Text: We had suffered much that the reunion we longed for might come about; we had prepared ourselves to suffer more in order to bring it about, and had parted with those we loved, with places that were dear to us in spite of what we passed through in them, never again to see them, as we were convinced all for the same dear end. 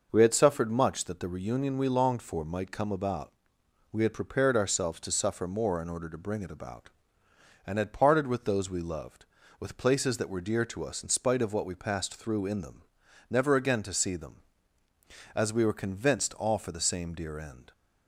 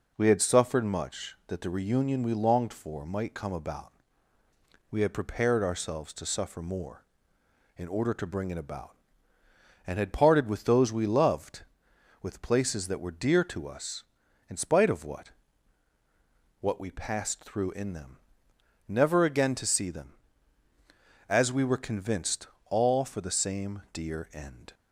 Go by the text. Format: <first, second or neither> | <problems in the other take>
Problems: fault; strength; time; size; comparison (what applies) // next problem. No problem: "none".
first | says "what" twice; at 16.5 s // pauses between "convinced" and "all"; slight; at 22.4 s; 0.24 s long